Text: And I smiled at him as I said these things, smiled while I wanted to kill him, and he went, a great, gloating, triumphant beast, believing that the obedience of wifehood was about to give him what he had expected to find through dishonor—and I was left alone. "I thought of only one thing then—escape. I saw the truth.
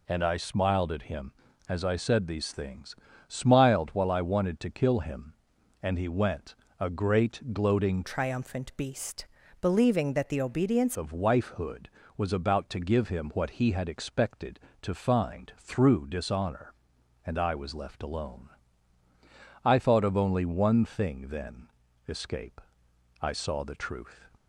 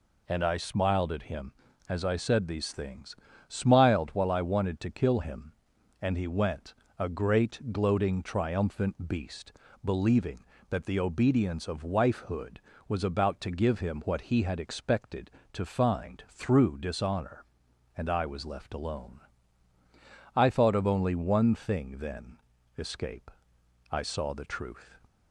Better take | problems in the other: second | changes voice from "triumphant" to "obedience"; from 8.0 to 10.9 s; 2.9 s long

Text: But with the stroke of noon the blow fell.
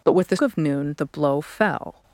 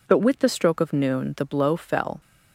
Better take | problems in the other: second | skips "stroke"; at 0.3 s

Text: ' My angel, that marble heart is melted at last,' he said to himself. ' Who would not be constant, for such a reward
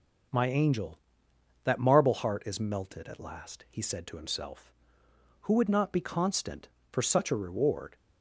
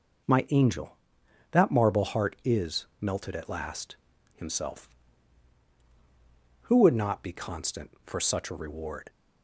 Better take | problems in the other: first | starts louder than the rest; until 1.8 s; 6.5 dB // pauses between "is" and "melted"; slight; at 2.8 s; 0.16 s long // skips "he said to"; at 4.1 s

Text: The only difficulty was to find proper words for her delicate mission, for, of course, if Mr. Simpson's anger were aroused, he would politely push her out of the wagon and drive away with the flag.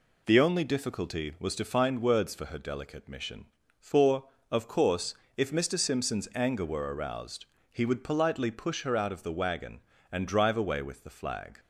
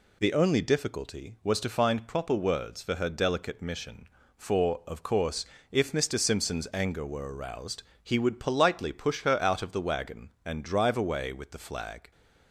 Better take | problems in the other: second | skips "proper"; at 2.0 s

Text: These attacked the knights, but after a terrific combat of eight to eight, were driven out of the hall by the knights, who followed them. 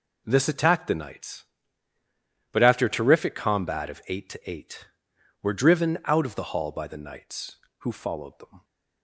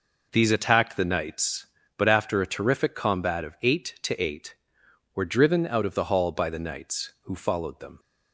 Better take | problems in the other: second | says "This" for "These"; at 0.2 s

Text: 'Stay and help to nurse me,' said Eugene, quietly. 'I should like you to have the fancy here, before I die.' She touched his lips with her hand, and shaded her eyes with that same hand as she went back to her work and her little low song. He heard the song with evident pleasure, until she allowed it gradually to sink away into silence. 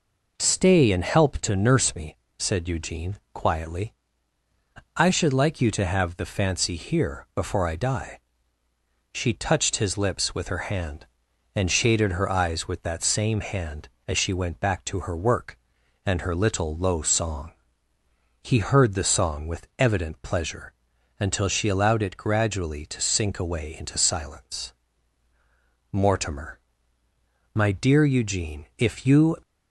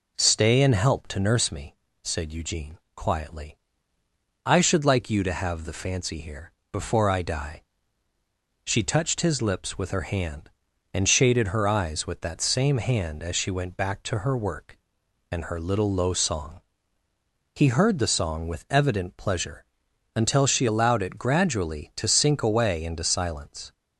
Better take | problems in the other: second | goes on to say "Mortimer My dear Eugene If you"; strong; from 25.9 s on; 3.4 s long

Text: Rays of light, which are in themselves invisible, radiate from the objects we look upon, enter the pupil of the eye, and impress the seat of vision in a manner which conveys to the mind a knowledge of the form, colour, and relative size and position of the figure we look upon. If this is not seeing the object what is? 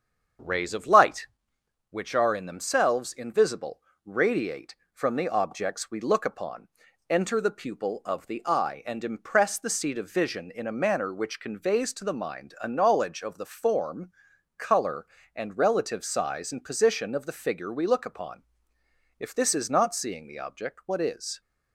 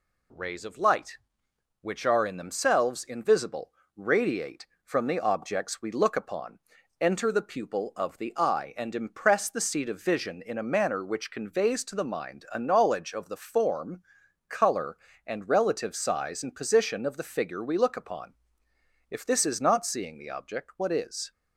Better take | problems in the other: second | starts louder than the rest; strong; until 1.3 s; 7.5 dB

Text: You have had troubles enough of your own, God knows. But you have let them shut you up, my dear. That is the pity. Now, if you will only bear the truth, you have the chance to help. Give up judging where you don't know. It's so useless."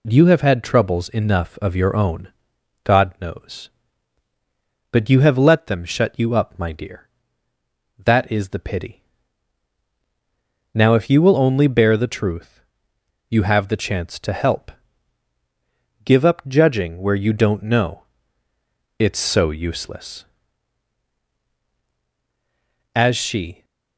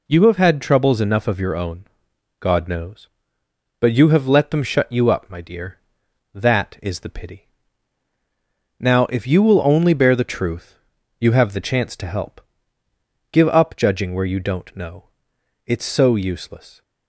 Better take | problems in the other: second | goes on to say "As she"; noticeable; from 22.9 s on; 0.70 s long

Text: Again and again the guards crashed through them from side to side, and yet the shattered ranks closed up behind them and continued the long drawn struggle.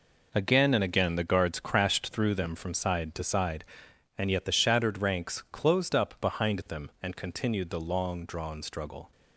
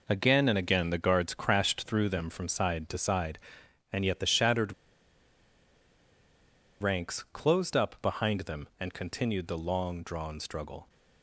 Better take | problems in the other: first | pauses between "shattered" and "ranks"; strong; at 4.7 s; 2.0 s long

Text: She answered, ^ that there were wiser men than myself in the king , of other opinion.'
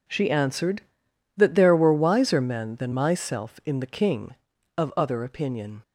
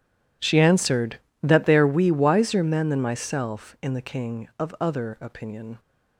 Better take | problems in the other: first | says "we" for "were"; at 1.8 s

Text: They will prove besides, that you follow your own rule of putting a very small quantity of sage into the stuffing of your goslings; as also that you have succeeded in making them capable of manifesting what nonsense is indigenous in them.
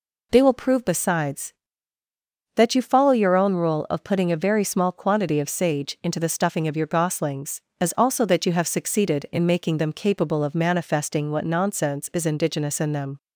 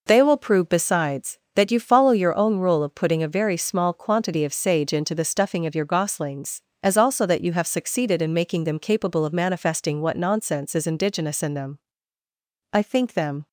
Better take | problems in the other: first | goes on to say "I think them"; noticeable; from 12.7 s on; 0.76 s long

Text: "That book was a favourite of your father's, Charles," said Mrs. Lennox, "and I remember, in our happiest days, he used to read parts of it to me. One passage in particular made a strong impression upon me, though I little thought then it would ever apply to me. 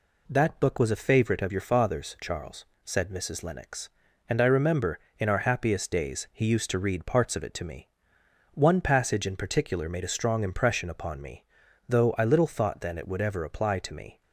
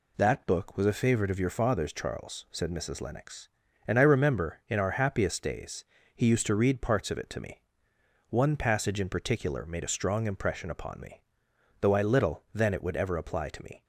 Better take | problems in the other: first | skips "thought"; at 12.4 s

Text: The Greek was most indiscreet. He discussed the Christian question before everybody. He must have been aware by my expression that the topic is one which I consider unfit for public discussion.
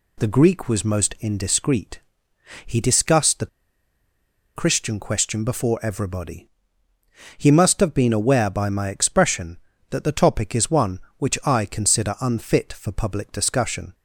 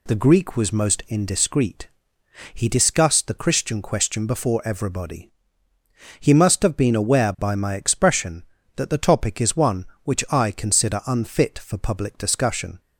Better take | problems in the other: second | pauses between "the" and "Christian"; at 3.4 s; 1.0 s long

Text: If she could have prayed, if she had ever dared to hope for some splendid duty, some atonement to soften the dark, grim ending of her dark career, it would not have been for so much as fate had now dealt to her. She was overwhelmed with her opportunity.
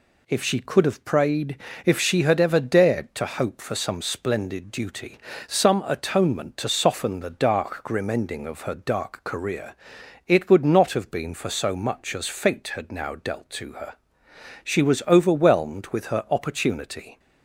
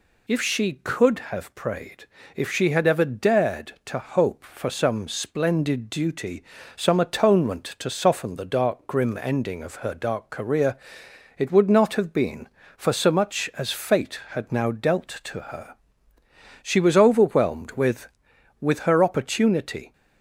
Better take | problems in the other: first | says "with" twice; at 18.6 s

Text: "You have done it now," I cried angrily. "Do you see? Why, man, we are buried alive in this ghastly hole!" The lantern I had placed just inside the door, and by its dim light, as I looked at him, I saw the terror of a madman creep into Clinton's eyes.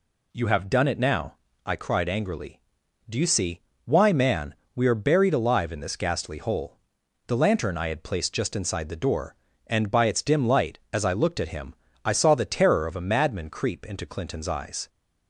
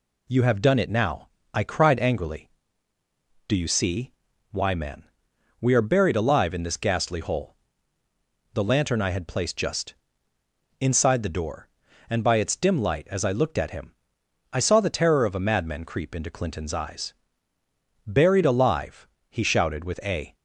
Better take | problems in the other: first | pauses between "just" and "inside"; noticeable; at 9.9 s; 0.86 s long // goes on to say "Buried alive he shouted with a"; strong; from 18.0 s on; 2.3 s long

